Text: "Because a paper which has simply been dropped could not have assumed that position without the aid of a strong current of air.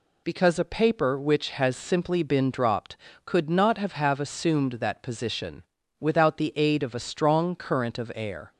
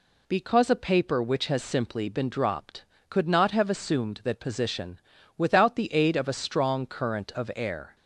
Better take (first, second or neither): second